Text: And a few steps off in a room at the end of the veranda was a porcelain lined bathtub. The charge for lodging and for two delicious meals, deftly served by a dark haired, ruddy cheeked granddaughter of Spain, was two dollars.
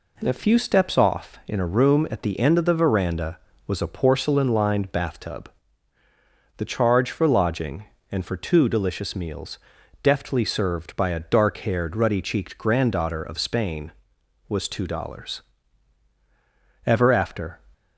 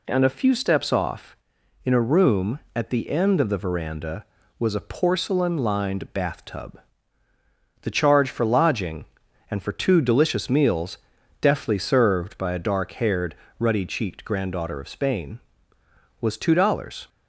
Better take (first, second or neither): second